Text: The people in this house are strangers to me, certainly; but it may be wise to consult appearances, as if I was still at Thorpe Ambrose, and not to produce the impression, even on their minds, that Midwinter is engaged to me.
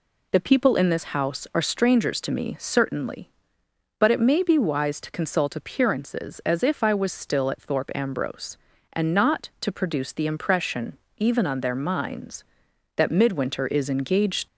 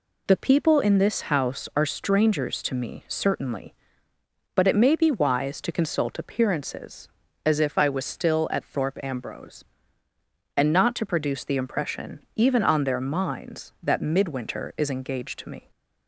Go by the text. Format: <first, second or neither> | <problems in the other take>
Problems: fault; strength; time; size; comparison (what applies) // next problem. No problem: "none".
second | stops before "to me"; at 14.4 s